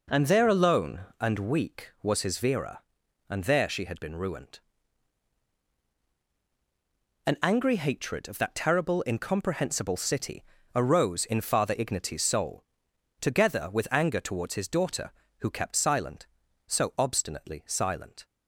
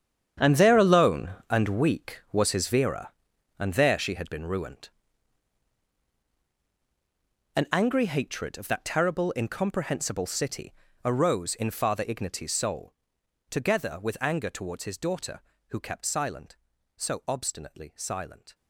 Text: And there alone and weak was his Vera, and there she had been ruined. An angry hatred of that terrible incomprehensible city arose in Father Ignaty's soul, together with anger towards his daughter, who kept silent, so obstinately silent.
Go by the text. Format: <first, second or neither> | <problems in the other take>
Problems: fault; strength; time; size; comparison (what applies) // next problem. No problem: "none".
first | gets quieter; strong; throughout; 13.5 dB // pauses between "city" and "arose"; slight; at 10.7 s; 0.32 s long; slight in the first